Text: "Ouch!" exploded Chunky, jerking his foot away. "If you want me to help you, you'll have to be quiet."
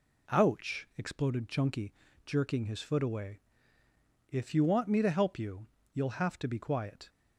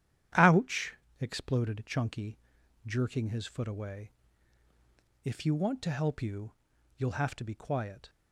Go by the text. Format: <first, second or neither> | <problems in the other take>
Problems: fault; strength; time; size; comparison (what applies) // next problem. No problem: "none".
first | starts louder than the rest; strong; until 1.6 s; 10.5 dB // skips "me"; at 5.8 s